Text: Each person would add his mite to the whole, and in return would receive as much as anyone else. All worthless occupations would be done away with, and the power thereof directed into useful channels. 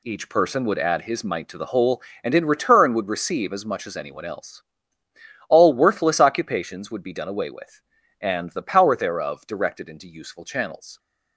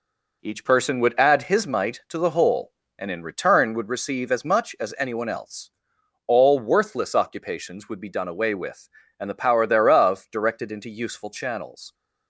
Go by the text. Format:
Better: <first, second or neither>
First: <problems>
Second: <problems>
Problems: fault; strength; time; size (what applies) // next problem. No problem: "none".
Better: first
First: none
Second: starts louder than the rest; noticeable; until 1.7 s; 4.5 dB